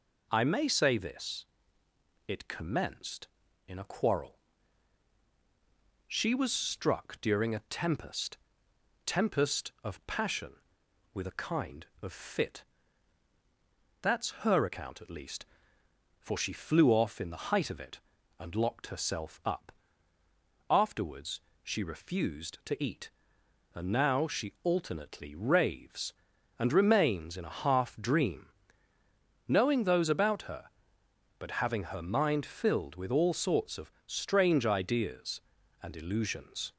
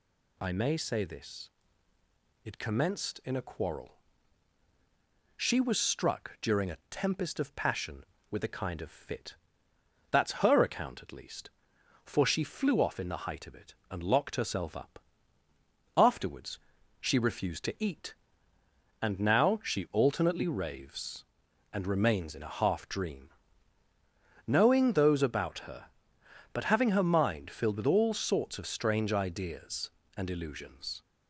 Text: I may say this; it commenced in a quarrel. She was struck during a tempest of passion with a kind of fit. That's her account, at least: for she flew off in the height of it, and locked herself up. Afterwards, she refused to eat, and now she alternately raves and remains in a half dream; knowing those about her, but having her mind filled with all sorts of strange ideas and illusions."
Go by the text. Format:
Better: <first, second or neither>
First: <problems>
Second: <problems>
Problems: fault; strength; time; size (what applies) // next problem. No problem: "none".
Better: second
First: says "tempest" twice; at 9.0 s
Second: none